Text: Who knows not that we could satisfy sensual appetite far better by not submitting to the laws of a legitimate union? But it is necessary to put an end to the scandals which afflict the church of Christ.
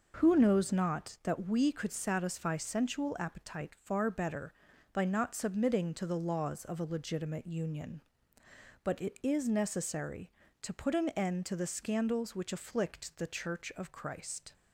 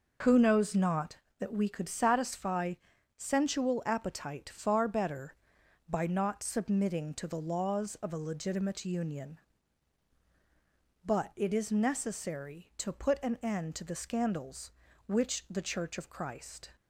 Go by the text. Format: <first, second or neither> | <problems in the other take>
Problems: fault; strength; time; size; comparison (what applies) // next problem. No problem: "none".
first | pauses between "satisfy" and "sensual"; at 2.7 s; 0.42 s long // skips "afflict"; at 15.4 s